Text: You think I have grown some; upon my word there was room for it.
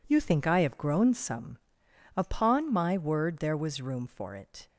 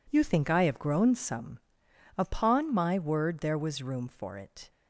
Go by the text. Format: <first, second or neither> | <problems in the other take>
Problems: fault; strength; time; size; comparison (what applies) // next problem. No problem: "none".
neither | none